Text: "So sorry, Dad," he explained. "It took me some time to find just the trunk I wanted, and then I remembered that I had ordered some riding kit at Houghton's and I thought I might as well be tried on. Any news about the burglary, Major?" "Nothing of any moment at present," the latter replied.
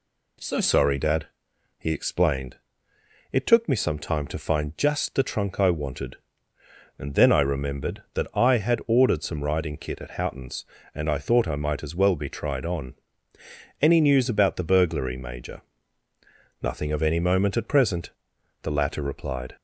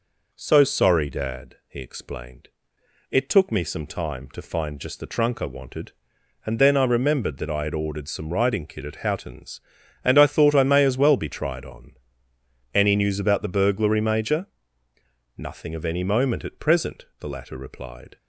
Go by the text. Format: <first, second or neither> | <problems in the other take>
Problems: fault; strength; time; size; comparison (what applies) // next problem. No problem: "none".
first | says "may" for "might"; at 10.6 s